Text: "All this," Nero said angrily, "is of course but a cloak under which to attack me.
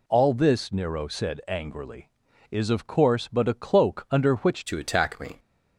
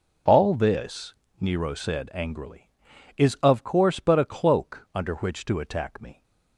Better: second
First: changes voice at "to"; from 4.6 s on; 0.7 s long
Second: none

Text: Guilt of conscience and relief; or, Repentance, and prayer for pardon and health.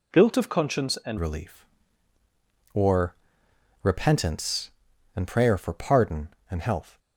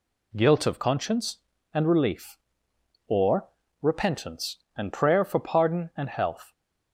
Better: second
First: changes voice at "relief"; from 1.1 s on; 5.8 s long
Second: none

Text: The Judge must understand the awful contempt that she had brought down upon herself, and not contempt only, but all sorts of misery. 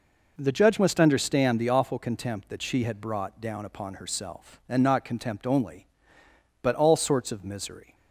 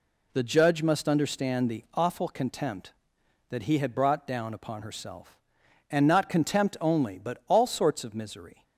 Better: first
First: none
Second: says "he" for "she"; at 3.6 s

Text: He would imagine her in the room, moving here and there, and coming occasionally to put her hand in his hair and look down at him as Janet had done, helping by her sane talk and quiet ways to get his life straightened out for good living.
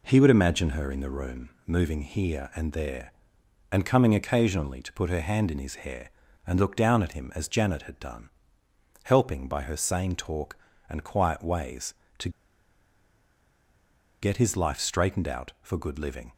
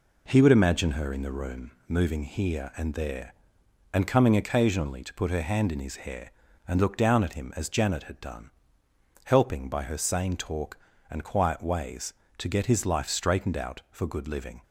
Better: second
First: pauses between "to" and "get"; strong; at 12.2 s; 1.9 s long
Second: none

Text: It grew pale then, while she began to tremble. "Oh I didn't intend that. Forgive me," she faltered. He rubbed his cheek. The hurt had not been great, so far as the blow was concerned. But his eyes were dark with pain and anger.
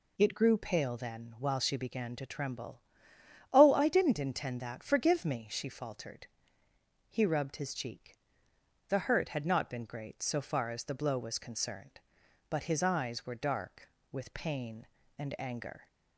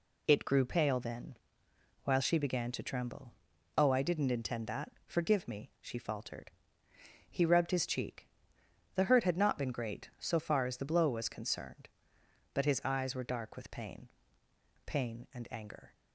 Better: first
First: none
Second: says "pain" twice; at 14.8 s

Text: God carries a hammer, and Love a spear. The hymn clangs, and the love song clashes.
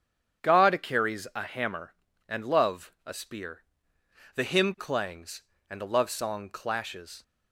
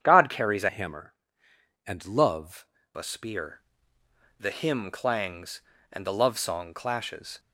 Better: first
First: starts louder than the rest; strong; until 1.5 s; 8.5 dB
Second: starts louder than the rest; strong; until 1.0 s; 8.5 dB // changes voice from "hammer" to "Love"; from 0.6 to 2.6 s; 2.0 s long

